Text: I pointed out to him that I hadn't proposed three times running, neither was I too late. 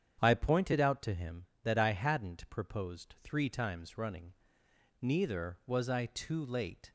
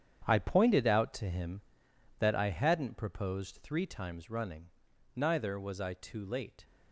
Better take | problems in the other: first | gets quieter; strong; throughout; 10 dB // starts louder than the rest; strong; until 1.2 s; 8.5 dB; strong in the first

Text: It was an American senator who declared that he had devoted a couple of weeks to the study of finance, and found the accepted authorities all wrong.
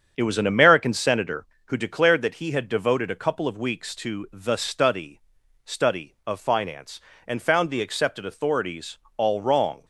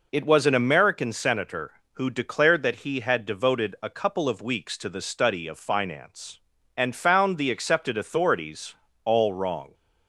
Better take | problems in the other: second | starts louder than the rest; strong; until 1.1 s; 7.5 dB // says "study" twice; at 5.6 s // pauses between "authorities" and "all"; slight; at 8.9 s; 0.18 s long; slight in the second

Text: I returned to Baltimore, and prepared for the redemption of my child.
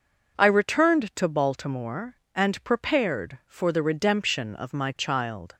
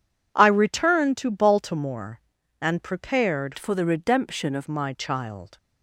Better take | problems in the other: first | changes voice from "for" to "of"; from 3.5 to 4.6 s; 1.1 s long

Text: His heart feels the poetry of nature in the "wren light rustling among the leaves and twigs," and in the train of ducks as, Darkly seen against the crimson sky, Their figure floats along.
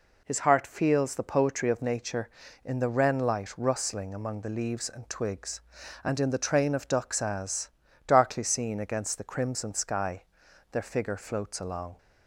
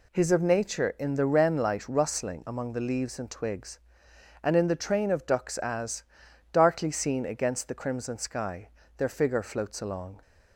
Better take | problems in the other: first | skips "heart feels the poetry"; at 0.3 s

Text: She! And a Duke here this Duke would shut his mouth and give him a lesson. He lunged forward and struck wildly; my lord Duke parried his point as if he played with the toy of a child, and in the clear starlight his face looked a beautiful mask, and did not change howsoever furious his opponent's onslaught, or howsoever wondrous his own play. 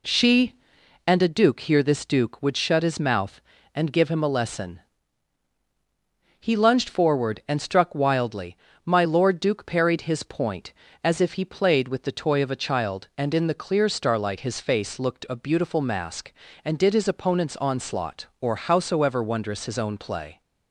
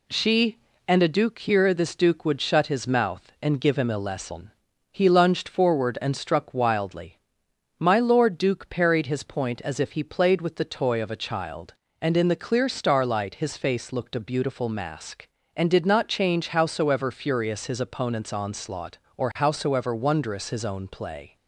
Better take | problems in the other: second | skips "not change howsoever furious"; at 16.9 s

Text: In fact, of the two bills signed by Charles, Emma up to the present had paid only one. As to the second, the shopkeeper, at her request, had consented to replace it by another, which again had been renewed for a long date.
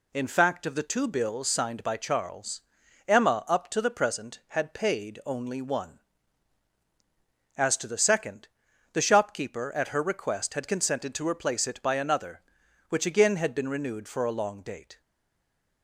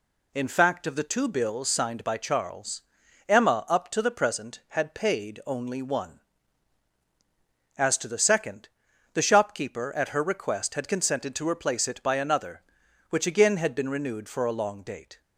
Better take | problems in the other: second | stays silent after the last word; slight; from 14.9 s on; 0.9 s long

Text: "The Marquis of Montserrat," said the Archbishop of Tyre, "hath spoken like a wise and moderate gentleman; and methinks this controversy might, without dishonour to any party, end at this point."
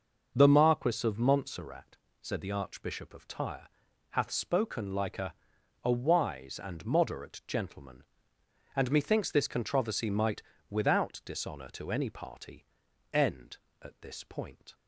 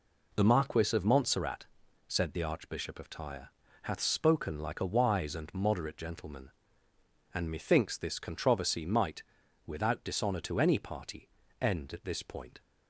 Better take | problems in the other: second | starts louder than the rest; noticeable; until 1.3 s; 6 dB // says "a" twice; at 5.8 s

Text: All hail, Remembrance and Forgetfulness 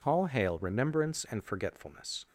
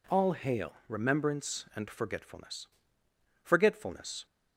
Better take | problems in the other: first | says "Forgetfulness" twice; at 3.4 s

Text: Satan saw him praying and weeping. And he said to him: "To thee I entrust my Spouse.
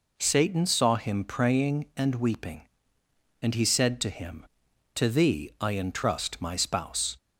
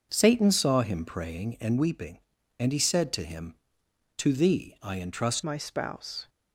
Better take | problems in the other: first | starts louder than the rest; until 1.1 s; 6 dB // changes voice at "my"; from 5.4 s on; 0.8 s long

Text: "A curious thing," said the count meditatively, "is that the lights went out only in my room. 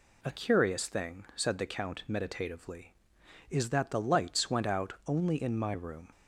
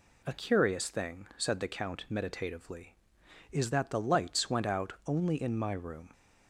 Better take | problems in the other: neither | none

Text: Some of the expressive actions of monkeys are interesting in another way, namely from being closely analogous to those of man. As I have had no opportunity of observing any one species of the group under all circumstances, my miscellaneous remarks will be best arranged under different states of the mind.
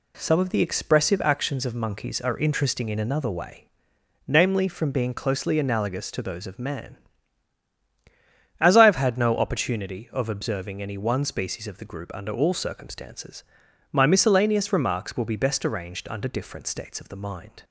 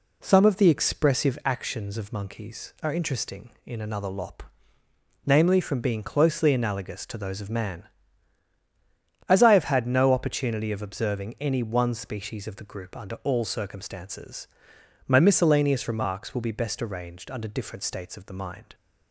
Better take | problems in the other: first | says "lop" for "way"; at 4.0 s

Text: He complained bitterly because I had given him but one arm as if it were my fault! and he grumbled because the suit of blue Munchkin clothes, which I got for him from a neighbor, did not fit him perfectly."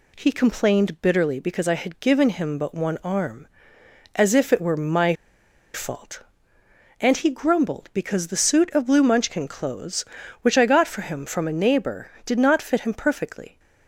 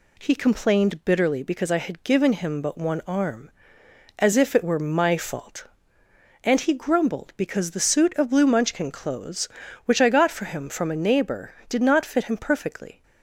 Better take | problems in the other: second | pauses between "my" and "fault"; noticeable; at 5.1 s; 0.61 s long

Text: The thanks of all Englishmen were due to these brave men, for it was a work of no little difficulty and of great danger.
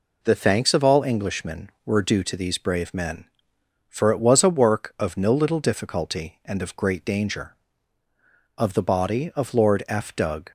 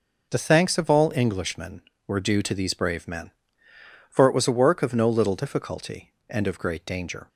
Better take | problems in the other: second | goes on to say "Of the body of Lord F Doug"; strong; from 8.5 s on; 1.9 s long

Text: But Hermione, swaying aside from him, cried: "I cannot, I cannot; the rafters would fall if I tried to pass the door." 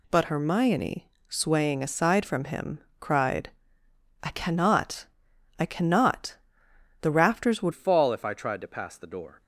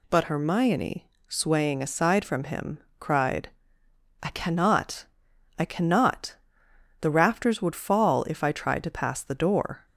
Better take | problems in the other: second | changes voice at "fall"; from 7.7 s on; 1.7 s long

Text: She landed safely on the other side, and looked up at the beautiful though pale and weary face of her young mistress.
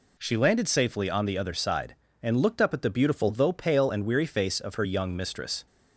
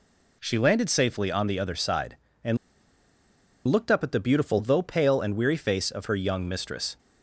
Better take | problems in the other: first | pauses between "and" and "looked"; at 2.5 s; 1.0 s long

